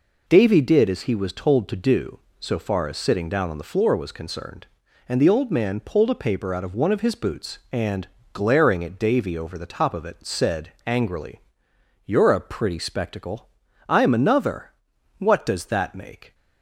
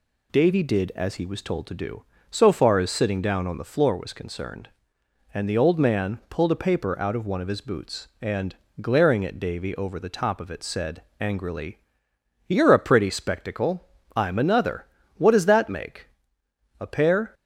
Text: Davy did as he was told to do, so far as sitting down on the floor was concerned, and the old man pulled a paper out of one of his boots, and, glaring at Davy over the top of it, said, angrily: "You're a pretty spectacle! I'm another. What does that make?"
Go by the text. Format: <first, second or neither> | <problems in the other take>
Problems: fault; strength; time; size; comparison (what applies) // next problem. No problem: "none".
first | goes on to say "A pair"; from 16.7 s on; 0.54 s long